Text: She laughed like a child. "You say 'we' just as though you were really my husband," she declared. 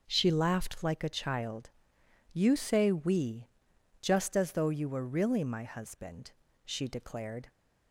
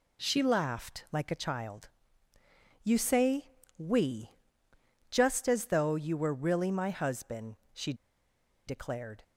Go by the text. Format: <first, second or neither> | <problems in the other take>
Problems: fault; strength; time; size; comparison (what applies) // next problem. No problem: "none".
first | pauses between "say" and "we"; slight; at 3.5 s; 0.26 s long // pauses between "we" and "just"; noticeable; at 4.3 s; 0.80 s long; noticeable in the first // pauses between "she" and "declared"; noticeable; at 7.9 s; 0.73 s long